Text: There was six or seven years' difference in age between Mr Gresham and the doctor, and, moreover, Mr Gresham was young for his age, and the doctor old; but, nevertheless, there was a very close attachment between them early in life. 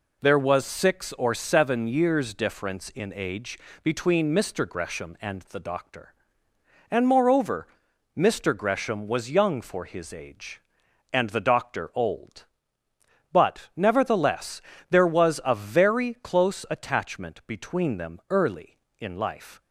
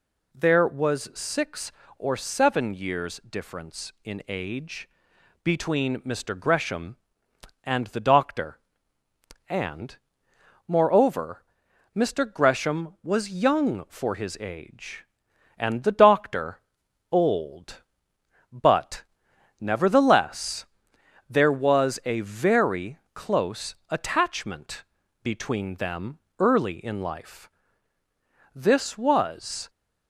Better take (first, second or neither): first